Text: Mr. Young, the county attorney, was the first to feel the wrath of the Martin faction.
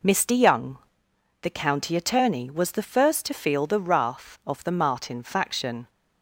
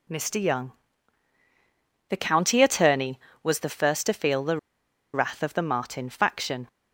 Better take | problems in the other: first | pauses between "the" and "wrath"; noticeable; at 4.5 s; 0.56 s long

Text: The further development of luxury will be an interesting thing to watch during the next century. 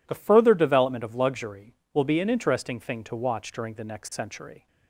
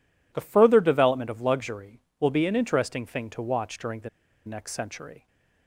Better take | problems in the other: first | pauses between "the" and "next"; at 4.0 s; 0.37 s long

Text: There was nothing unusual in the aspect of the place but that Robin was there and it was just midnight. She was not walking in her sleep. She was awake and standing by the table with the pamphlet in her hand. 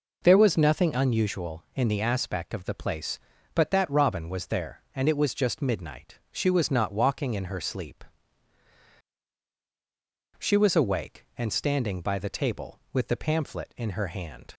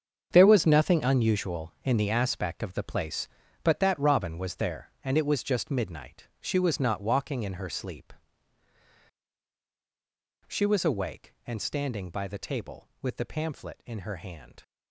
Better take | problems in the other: first | gets quieter; strong; throughout; 13 dB

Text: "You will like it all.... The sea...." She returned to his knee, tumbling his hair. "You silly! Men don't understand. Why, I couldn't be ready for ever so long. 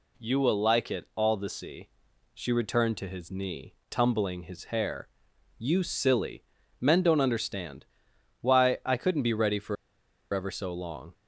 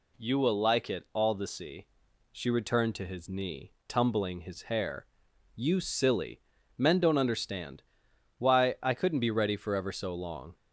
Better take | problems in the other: second | pauses between "for" and "ever"; noticeable; at 9.7 s; 0.58 s long

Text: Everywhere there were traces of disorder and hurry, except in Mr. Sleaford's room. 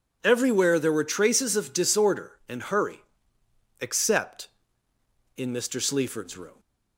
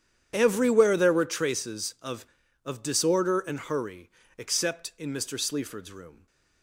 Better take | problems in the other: first | starts louder than the rest; strong; until 1.3 s; 9.5 dB // says "of" twice; at 2.6 s

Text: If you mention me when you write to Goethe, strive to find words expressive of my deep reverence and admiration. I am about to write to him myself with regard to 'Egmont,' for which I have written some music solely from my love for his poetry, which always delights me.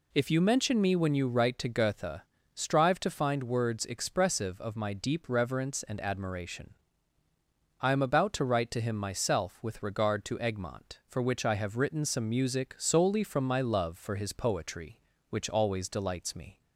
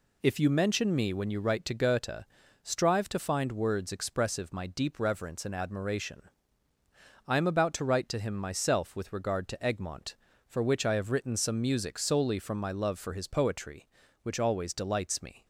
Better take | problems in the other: first | skips "of"; at 4.5 s

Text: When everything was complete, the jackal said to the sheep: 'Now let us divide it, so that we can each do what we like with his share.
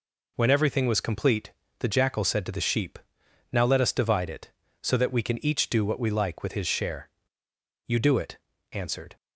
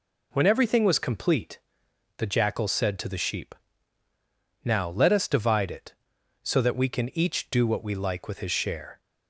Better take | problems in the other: second | goes on to say "You do it answered"; noticeable; from 7.8 s on; 1.3 s long

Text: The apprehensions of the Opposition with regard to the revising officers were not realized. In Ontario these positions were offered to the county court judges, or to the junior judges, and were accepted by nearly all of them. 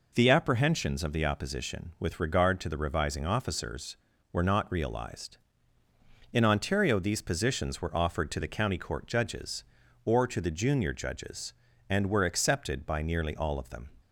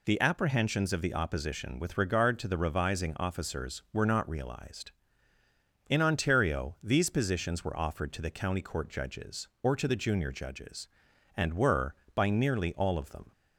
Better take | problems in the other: first | skips "accepted"; at 12.0 s

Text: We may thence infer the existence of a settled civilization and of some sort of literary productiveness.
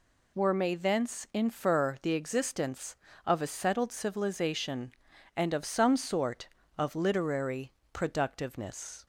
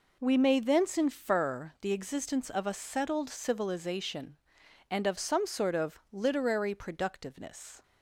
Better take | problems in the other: second | says "Were" for "We"; at 0.3 s // pauses between "literary" and "productiveness"; slight; at 7.7 s; 0.22 s long

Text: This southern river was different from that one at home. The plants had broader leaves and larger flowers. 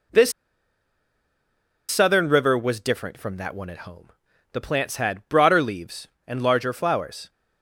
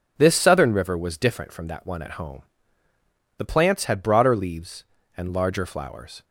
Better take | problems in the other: second | pauses between "This" and "southern"; strong; at 0.3 s; 1.5 s long

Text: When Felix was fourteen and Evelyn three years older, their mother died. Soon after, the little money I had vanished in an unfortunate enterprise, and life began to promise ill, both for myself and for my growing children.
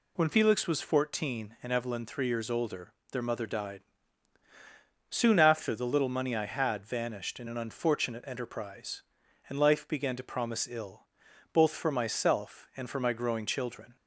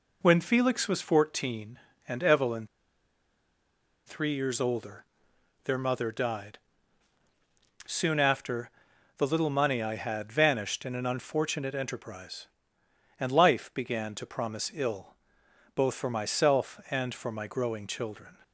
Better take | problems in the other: first | pauses between "Evelyn" and "three"; strong; at 2.6 s; 1.3 s long

